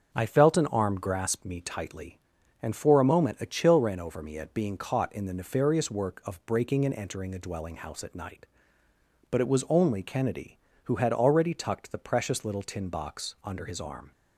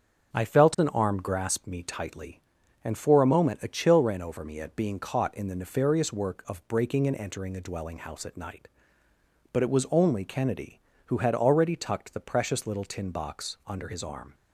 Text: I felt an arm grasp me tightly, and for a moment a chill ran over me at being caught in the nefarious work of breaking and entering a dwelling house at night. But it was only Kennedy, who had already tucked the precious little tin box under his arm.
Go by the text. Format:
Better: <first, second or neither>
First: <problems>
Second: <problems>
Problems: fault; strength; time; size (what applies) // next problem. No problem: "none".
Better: neither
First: starts louder than the rest; until 1.1 s; 6.5 dB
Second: starts louder than the rest; until 1.3 s; 6.5 dB